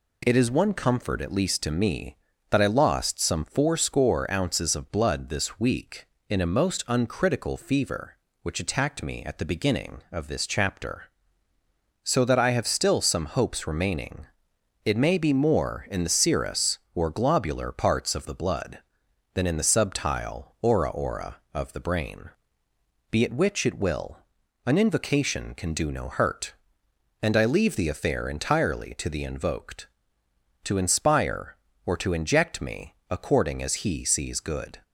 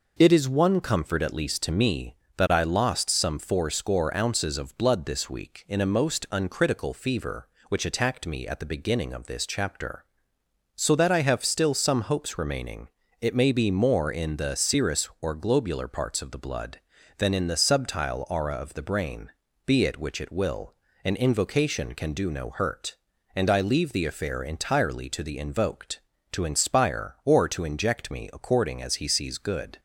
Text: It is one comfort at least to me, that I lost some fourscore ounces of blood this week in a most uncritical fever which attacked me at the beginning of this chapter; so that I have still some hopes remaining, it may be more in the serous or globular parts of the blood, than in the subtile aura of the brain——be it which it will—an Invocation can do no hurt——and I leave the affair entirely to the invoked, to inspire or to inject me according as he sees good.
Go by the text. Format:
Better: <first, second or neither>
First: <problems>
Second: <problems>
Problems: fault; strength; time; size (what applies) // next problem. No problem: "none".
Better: second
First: says "aura" twice; at 20.9 s // pauses between "me" and "according"; slight; at 32.9 s; 0.16 s long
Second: none